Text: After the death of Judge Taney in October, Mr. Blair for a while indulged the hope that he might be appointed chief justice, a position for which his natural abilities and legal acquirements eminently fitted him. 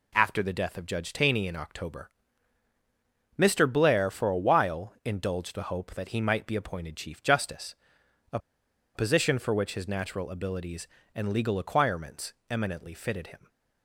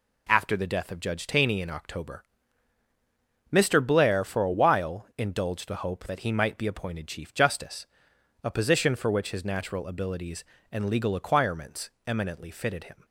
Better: second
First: pauses between "a" and "position"; noticeable; at 8.3 s; 0.57 s long // pauses between "acquirements" and "eminently"; slight; at 12.3 s; 0.16 s long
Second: pauses between "acquirements" and "eminently"; slight; at 11.9 s; 0.16 s long

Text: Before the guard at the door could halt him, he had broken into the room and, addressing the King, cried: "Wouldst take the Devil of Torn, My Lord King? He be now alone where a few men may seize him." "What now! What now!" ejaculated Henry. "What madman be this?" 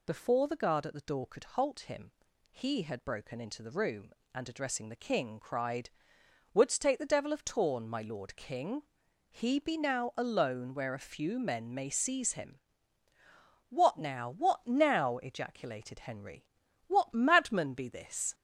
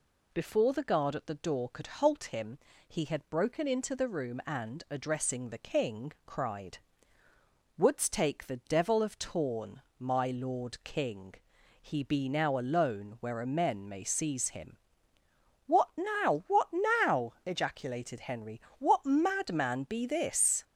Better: first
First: none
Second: skips "few"; at 13.4 s

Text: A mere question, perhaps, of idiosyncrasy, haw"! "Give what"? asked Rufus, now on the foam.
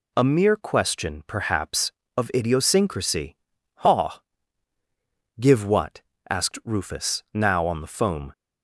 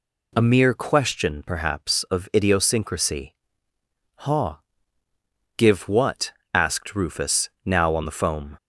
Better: neither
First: none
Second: none

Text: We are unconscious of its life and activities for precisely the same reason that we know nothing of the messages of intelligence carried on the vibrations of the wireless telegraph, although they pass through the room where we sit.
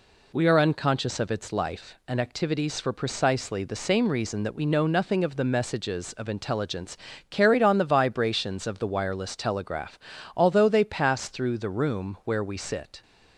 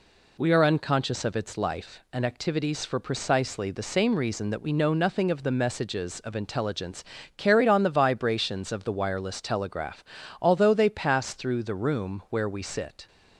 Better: neither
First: pauses between "intelligence" and "carried"; slight; at 6.9 s; 0.34 s long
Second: pauses between "intelligence" and "carried"; slight; at 7.0 s; 0.34 s long

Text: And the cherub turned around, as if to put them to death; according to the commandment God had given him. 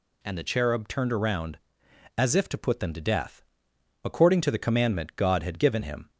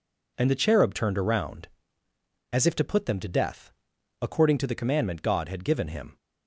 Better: neither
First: none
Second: none

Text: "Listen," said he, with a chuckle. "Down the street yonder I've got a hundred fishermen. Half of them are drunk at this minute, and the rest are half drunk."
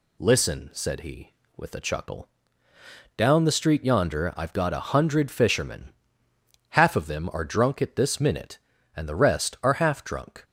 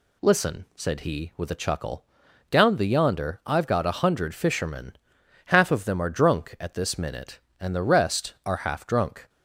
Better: first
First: none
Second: skips "street"; at 2.8 s

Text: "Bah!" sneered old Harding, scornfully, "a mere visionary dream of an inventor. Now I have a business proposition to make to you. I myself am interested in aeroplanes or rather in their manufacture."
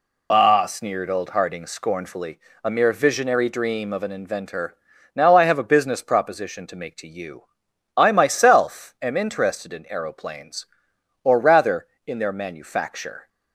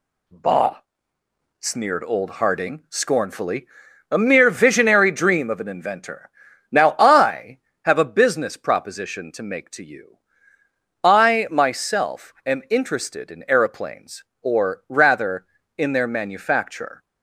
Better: second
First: loses the start of "Bah"; at 0.3 s; 60 ms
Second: none

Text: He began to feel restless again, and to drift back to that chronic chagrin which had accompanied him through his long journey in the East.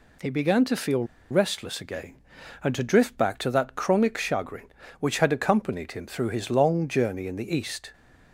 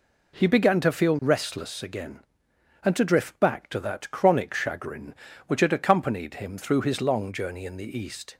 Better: second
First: pauses between "feel" and "restless"; slight; at 1.0 s; 0.26 s long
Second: none

